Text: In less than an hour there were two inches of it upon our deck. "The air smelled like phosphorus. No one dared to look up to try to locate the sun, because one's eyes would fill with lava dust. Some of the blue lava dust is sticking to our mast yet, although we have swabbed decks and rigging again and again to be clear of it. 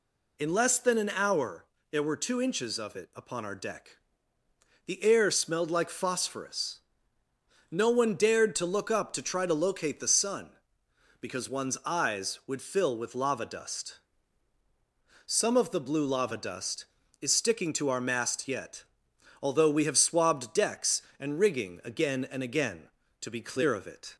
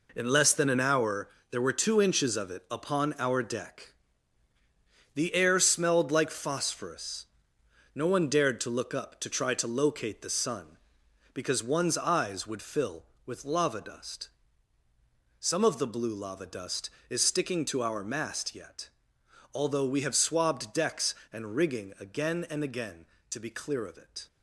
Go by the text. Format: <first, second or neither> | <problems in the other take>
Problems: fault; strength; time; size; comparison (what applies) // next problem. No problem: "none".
first | gets quieter; strong; throughout; 8.5 dB // pauses between "hour" and "there"; slight; at 1.2 s; 0.22 s long; slight in the first